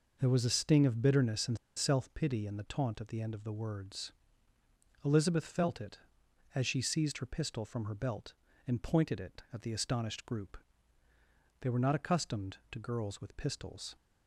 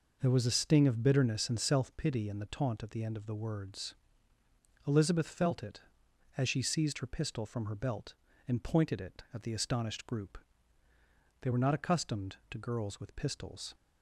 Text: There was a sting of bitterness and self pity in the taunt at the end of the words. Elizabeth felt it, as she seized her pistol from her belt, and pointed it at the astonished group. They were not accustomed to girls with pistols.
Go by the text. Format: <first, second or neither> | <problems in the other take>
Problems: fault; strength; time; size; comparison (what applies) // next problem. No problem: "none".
second | pauses between "and" and "self"; slight; at 1.5 s; 0.19 s long